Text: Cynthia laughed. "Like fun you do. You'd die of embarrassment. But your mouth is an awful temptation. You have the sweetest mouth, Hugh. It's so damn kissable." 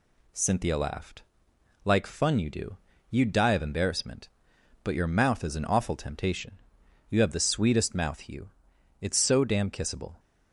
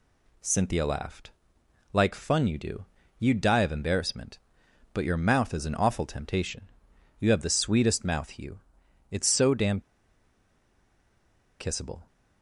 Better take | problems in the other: first | pauses between "damn" and "kissable"; strong; at 9.8 s; 1.7 s long

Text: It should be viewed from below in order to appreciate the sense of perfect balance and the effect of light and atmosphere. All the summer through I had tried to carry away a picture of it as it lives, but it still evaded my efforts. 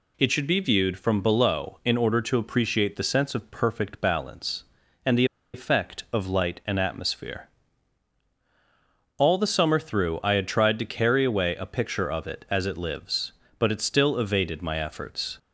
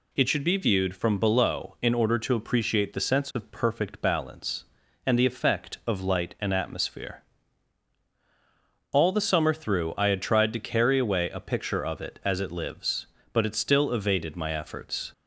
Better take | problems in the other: second | pauses between "the" and "effect"; slight; at 5.2 s; 0.29 s long

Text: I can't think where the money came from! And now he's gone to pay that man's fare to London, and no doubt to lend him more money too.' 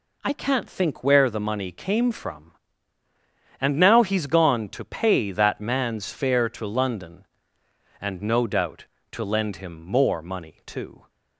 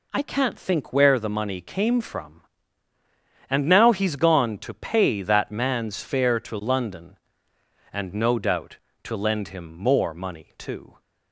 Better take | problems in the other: neither | none

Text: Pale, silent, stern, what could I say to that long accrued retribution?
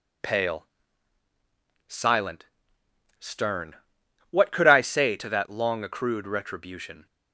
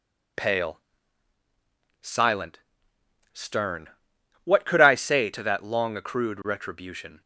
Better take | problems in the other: neither | none

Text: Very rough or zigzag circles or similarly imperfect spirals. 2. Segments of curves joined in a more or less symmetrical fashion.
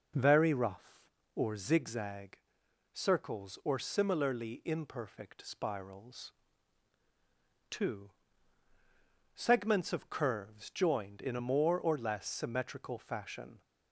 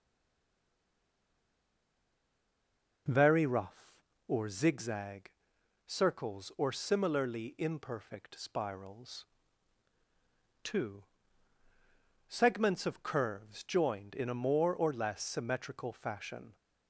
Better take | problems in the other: first | stays silent before the first word; strong; until 3.0 s; 3.0 s long // pauses between "zigzag" and "circles"; noticeable; at 5.3 s; 0.54 s long; noticeable in the first

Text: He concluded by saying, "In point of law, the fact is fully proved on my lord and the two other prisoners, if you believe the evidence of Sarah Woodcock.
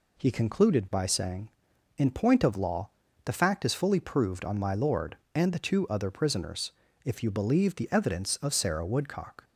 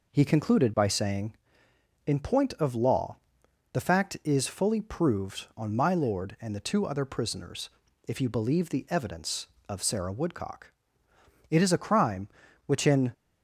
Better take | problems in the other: first | goes on to say "It is a crime which in"; from 11.4 s on; 1.6 s long

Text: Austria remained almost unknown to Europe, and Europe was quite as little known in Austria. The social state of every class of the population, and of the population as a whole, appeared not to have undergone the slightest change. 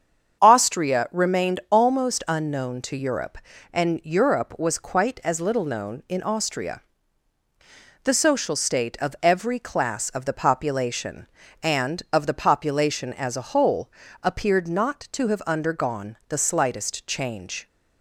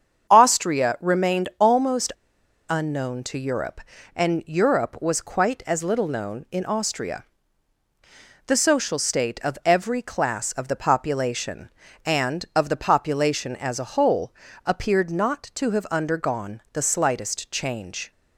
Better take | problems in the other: first | starts louder than the rest; strong; until 1.3 s; 7.5 dB; strong in the first // pauses between "almost" and "unknown"; noticeable; at 2.1 s; 0.59 s long

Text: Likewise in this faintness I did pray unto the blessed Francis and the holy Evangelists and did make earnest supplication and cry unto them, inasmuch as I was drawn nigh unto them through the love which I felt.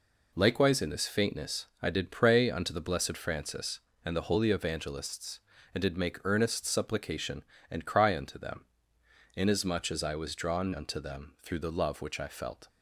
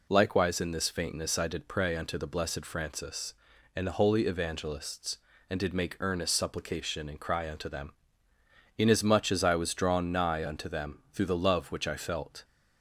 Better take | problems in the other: second | pauses between "faintness" and "I"; slight; at 1.6 s; 0.16 s long // skips "nigh"; at 10.7 s

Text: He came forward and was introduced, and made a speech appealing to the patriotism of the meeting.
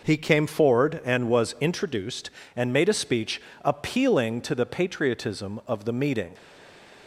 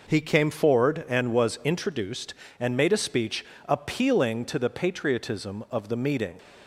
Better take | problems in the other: second | pauses between "speech" and "appealing"; slight; at 3.3 s; 0.24 s long; slight in the second // stays silent after the last word; slight; from 6.3 s on; 0.7 s long

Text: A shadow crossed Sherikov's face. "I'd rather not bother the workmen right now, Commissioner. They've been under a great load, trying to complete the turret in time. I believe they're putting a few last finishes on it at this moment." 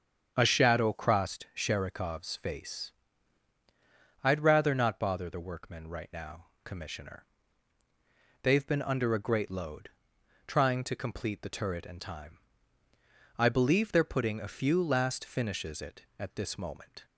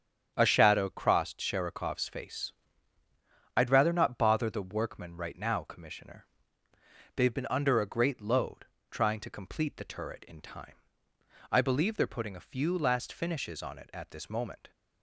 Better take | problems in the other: second | starts louder than the rest; strong; until 1.3 s; 7.5 dB; strong in the second // skips "on"; at 15.8 s

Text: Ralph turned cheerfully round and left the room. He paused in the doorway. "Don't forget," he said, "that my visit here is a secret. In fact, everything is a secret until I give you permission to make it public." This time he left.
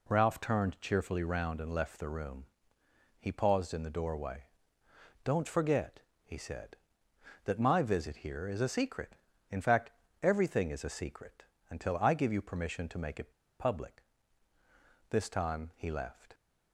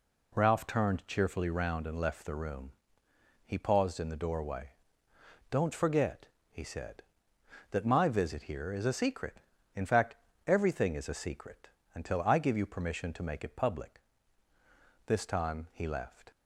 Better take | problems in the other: second | pauses between "secret" and "until"; slight; at 11.4 s; 0.26 s long; slight in the second // pauses between "it" and "public"; slight; at 13.3 s; 0.28 s long

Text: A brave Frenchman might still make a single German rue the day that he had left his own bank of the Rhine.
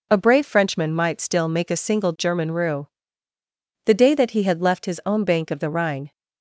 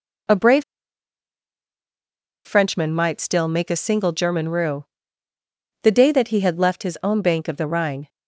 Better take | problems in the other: first | pauses between "brave" and "Frenchman"; strong; at 0.6 s; 1.8 s long // pauses between "rue" and "the"; noticeable; at 4.8 s; 0.98 s long; noticeable in the first

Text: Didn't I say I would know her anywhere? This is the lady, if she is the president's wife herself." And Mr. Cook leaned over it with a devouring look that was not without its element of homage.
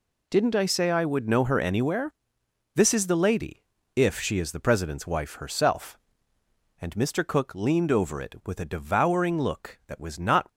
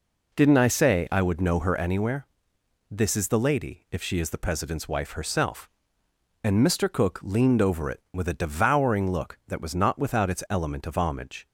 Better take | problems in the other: second | stops before "without its element of homage"; at 10.4 s

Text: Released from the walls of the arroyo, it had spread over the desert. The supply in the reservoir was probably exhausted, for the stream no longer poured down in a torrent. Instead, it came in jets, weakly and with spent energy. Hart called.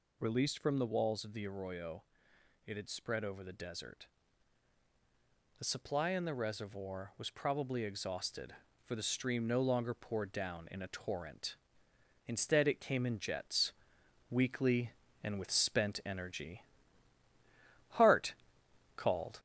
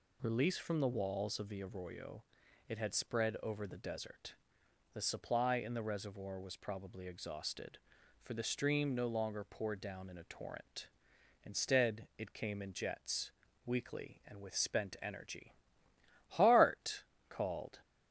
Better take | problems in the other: second | gets louder; slight; throughout; 2.5 dB // pauses between "Hart" and "called"; noticeable; at 18.3 s; 0.64 s long; slight in the second

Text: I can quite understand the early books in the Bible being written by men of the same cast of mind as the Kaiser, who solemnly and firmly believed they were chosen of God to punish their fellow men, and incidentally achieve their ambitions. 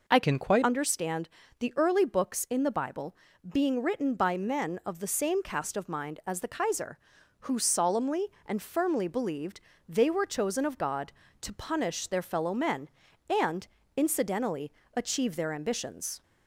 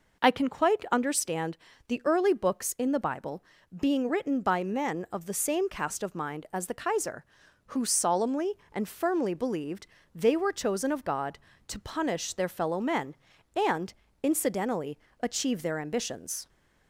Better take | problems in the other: second | changes voice from "can" to "quite"; from 0.2 to 0.6 s; 0.4 s long // pauses between "understand" and "the"; slight; at 1.2 s; 0.30 s long; slight in the second // pauses between "Bible" and "being"; slight; at 3.1 s; 0.36 s long; slight in the second // pauses between "believed" and "they"; slight; at 9.5 s; 0.28 s long; slight in the second // pauses between "and" and "incidentally"; slight; at 13.6 s; 0.30 s long; slight in the second // pauses between "incidentally" and "achieve"; slight; at 14.6 s; 0.26 s long; slight in the second

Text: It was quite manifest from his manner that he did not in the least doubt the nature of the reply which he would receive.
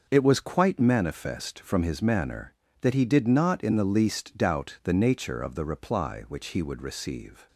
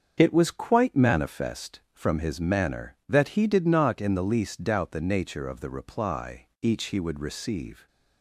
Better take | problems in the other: first | starts louder than the rest; until 1.1 s; 7 dB // says "each" for "which"; at 6.6 s

